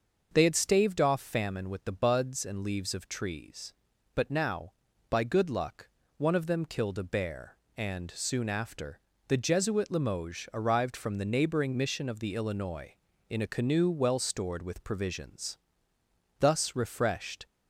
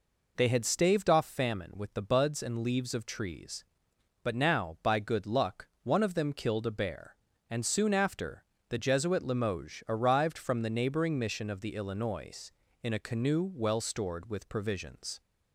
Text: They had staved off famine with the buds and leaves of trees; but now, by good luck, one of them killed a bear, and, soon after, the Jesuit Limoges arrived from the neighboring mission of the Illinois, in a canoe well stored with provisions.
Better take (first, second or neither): second